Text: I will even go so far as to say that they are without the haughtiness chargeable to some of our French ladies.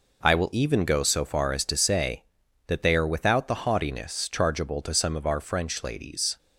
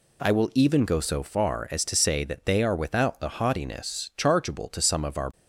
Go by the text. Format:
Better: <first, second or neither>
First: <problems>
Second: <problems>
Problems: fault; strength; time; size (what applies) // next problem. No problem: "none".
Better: first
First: none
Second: stops before "French ladies"; at 5.3 s